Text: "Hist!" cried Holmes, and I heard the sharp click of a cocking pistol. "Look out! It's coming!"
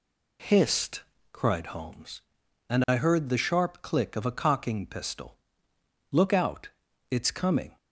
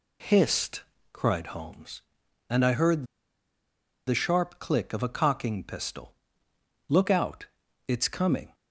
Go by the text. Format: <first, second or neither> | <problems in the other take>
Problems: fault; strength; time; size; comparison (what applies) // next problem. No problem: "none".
first | pauses between "heard" and "the"; at 3.0 s; 1.0 s long